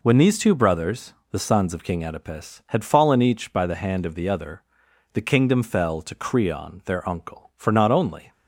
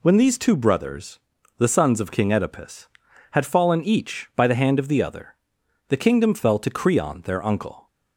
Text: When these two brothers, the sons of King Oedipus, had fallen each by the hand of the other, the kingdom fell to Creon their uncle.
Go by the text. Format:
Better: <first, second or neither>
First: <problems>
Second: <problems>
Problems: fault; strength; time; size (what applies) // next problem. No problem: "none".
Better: second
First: goes on to say "For not only"; noticeable; from 7.5 s on; 0.76 s long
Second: none